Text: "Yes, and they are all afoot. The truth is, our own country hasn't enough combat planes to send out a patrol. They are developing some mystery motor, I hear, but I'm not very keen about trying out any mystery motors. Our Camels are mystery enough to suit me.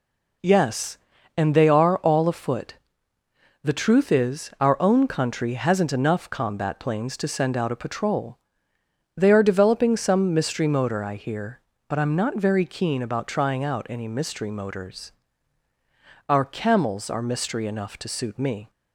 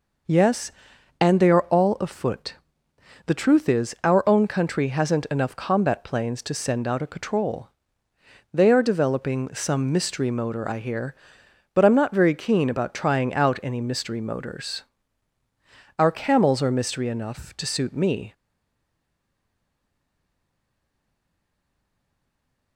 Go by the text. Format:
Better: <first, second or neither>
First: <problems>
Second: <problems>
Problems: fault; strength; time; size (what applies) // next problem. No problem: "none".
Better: first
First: none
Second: stays silent after the last word; strong; from 18.3 s on; 4.4 s long